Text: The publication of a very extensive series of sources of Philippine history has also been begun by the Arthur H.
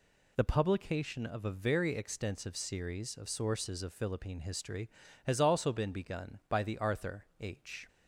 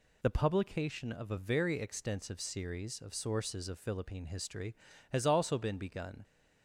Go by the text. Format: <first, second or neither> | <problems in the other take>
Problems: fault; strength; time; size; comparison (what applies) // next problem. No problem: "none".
first | stops before "by the Arthur H"; at 6.2 s